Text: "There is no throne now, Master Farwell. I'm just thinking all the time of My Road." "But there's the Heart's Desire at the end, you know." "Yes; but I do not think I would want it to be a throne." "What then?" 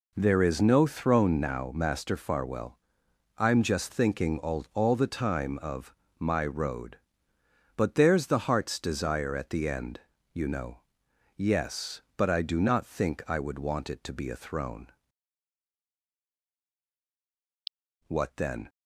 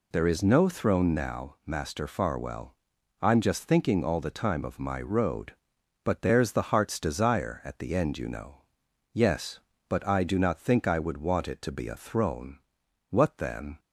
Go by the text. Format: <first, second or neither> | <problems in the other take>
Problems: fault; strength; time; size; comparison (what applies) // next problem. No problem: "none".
second | says "all" twice; at 4.7 s // pauses between "of" and "My"; slight; at 5.9 s; 0.24 s long